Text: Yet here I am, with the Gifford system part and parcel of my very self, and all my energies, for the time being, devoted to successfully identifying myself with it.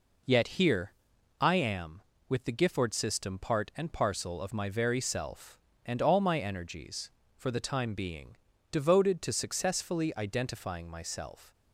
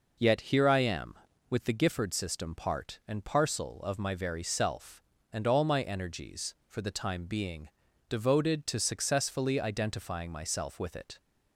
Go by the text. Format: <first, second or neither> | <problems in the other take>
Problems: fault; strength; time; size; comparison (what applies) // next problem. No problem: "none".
second | pauses between "here" and "I"; noticeable; at 0.9 s; 0.48 s long // stops before "with it"; at 11.5 s